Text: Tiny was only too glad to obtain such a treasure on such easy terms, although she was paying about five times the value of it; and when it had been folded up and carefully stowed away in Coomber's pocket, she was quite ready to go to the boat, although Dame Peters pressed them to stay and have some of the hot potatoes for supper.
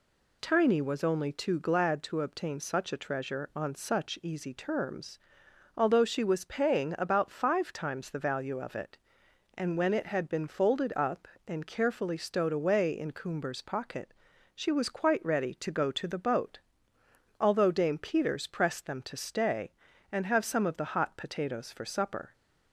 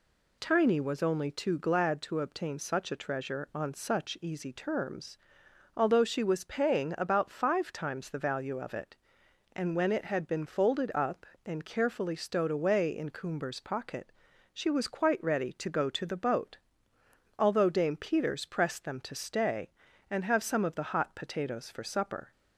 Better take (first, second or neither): neither